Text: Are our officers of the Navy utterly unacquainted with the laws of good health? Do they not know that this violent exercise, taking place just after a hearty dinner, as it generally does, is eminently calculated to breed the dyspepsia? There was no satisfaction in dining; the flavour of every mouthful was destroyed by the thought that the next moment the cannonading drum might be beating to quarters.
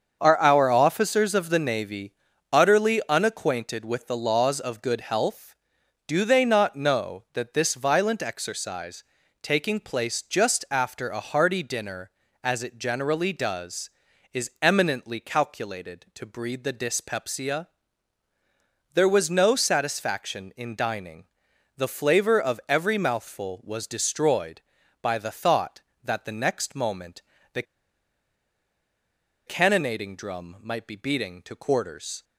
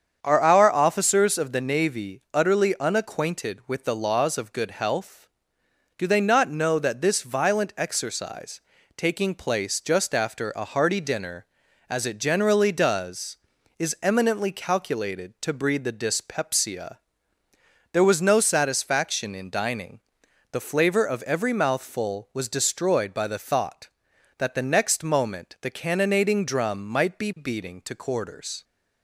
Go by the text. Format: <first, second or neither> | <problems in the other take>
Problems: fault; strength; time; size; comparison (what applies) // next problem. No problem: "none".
second | starts louder than the rest; until 1.2 s; 7 dB; strong in the second // pauses between "Navy" and "utterly"; at 2.1 s; 0.38 s long // pauses between "moment" and "the"; slight; at 27.2 s; 0.34 s long // pauses between "the" and "cannonading"; strong; at 27.6 s; 1.8 s long